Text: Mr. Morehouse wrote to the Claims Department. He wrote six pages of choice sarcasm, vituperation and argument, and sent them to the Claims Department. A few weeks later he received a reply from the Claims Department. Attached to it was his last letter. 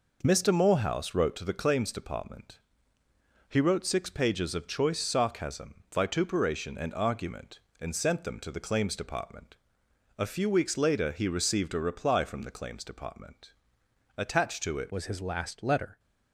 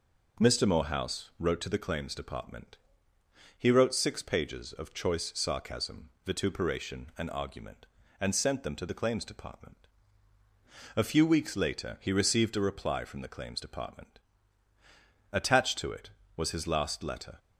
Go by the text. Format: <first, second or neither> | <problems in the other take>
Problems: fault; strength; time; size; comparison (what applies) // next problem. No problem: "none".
second | changes voice at "was"; from 14.9 s on; 1.0 s long